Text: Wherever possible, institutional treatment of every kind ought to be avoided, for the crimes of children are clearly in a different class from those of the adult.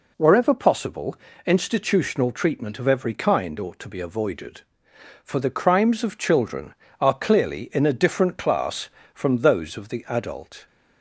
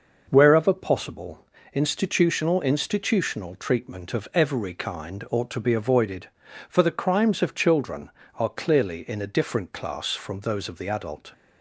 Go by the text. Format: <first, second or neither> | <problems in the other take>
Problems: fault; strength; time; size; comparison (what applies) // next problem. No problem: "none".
first | says "institutional" twice; at 2.6 s